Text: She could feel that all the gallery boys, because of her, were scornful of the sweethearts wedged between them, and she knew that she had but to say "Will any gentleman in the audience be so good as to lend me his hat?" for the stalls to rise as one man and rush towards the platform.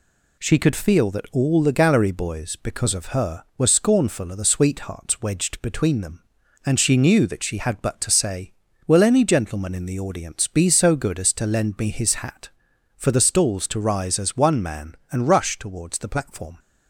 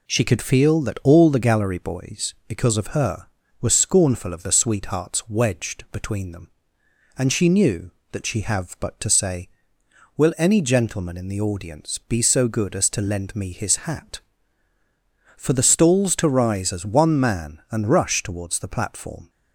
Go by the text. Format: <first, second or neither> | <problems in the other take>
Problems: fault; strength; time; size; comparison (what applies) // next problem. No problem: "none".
first | says "have" for "had"; at 8.4 s